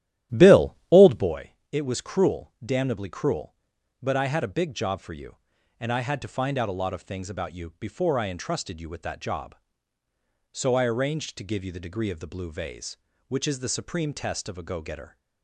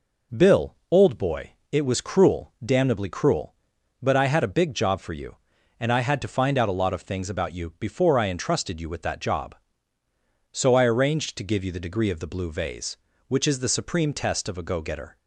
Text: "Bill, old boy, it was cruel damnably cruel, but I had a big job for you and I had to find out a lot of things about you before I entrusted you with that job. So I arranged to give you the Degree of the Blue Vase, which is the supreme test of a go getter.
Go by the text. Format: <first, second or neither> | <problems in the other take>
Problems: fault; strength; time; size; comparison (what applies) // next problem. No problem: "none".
second | starts louder than the rest; strong; until 1.4 s; 13 dB